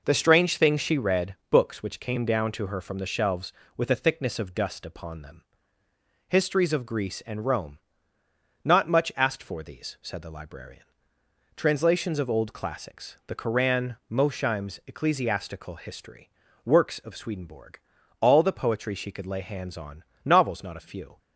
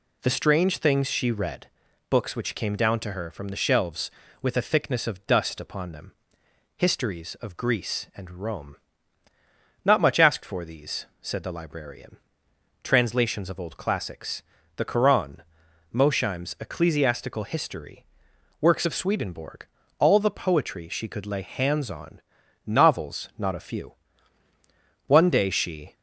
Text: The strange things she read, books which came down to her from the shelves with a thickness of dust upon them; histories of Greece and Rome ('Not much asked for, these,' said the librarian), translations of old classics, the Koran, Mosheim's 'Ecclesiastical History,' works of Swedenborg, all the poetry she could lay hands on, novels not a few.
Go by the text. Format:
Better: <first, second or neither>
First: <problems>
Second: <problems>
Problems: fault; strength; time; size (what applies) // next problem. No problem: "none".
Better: first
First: none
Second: goes on to say "One day she"; noticeable; from 25.0 s on; 0.88 s long